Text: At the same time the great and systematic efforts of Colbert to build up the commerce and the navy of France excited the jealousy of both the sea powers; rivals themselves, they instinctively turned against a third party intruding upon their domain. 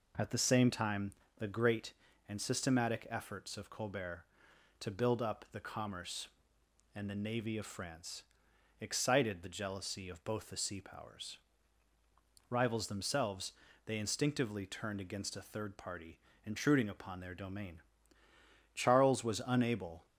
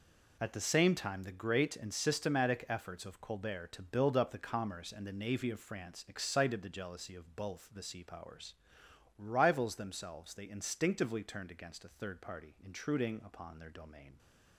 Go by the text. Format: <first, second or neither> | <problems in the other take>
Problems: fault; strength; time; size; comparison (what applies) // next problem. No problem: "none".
second | pauses between "time" and "the"; slight; at 1.1 s; 0.26 s long // pauses between "France" and "excited"; noticeable; at 8.2 s; 0.58 s long // pauses between "party" and "intruding"; slight; at 16.1 s; 0.28 s long // goes on to say "Charles was unable"; from 18.7 s on; 1.3 s long